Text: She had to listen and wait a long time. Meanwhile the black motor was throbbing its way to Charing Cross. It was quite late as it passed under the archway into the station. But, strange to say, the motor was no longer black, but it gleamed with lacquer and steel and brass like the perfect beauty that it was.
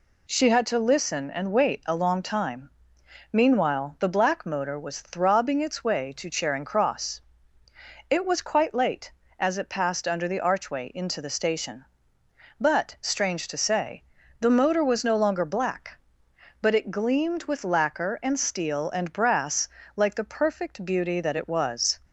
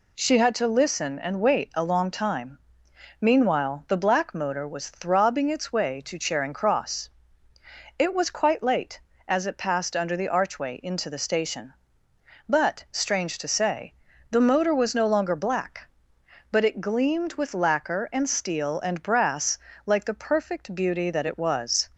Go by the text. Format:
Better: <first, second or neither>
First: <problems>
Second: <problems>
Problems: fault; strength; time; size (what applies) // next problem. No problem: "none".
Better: neither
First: pauses between "brass" and "like"; slight; at 19.6 s; 0.28 s long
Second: pauses between "brass" and "like"; slight; at 19.5 s; 0.28 s long